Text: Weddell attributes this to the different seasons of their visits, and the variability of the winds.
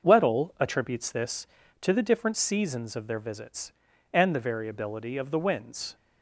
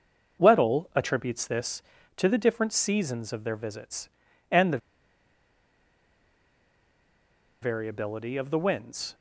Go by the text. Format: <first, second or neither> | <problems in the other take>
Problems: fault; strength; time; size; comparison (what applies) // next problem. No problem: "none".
first | starts louder than the rest; noticeable; until 1.4 s; 6 dB; noticeable in the first // pauses between "the" and "variability"; strong; at 4.7 s; 2.8 s long